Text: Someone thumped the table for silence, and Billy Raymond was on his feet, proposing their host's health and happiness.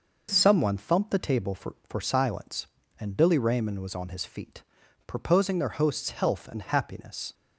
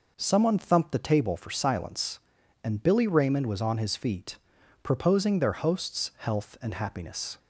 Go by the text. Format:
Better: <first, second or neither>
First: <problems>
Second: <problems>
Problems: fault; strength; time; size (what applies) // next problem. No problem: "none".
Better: second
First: says "for" twice; at 1.8 s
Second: none